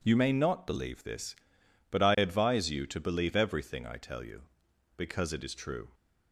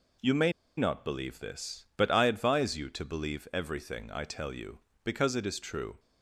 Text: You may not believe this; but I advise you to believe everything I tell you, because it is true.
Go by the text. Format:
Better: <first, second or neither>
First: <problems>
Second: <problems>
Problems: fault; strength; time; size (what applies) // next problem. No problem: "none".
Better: first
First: none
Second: pauses between "may" and "not"; slight; at 0.5 s; 0.26 s long